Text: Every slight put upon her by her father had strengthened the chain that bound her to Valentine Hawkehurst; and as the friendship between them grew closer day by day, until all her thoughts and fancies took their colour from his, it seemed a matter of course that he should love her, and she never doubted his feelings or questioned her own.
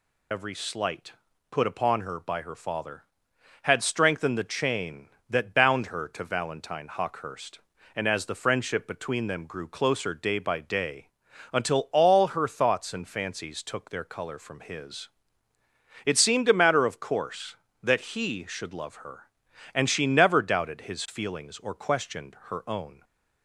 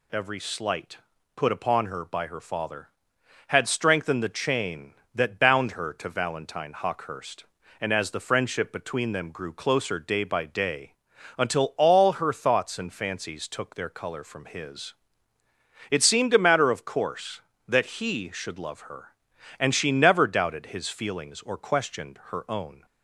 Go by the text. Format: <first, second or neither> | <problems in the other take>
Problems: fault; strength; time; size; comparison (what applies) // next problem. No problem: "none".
second | loses the start of "Every"; at 0.3 s; 40 ms // pauses between "slight" and "put"; at 1.1 s; 0.40 s long; also in the second